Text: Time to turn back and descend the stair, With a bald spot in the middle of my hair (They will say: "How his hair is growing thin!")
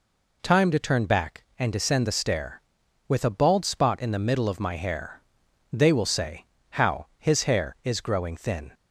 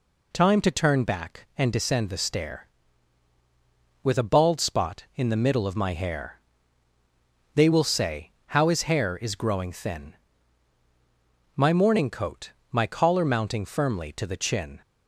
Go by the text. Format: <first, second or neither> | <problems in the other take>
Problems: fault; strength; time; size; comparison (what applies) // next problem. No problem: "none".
first | goes on to say "My morning coat my collar mounting firmly to the chin"; strong; from 11.5 s on; 3.2 s long